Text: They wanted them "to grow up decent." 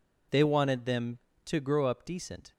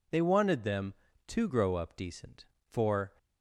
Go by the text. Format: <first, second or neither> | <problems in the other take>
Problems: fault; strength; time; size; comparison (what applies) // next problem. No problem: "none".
first | goes on to say "For"; slight; from 2.6 s on; 0.42 s long